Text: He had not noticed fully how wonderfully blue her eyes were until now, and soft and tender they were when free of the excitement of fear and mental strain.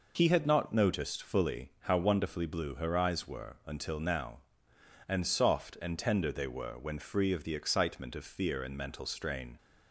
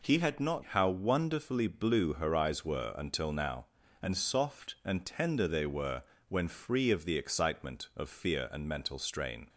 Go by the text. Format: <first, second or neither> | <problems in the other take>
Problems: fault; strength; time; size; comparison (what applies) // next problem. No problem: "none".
first | skips "noticed fully"; at 0.6 s // pauses between "were" and "when"; slight; at 6.0 s; 0.26 s long